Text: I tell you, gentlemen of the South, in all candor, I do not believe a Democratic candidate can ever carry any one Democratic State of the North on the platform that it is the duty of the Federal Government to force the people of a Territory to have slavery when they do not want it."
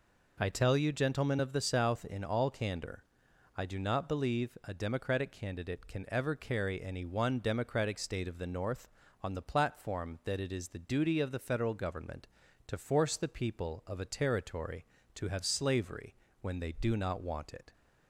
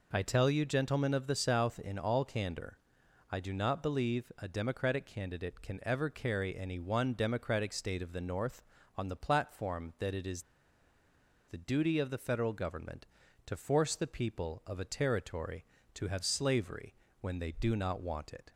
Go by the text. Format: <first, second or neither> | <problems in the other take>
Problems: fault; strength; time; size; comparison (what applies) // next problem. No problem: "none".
first | pauses between "is" and "the"; at 10.4 s; 1.0 s long // pauses between "slavery" and "when"; slight; at 16.9 s; 0.30 s long; slight in the first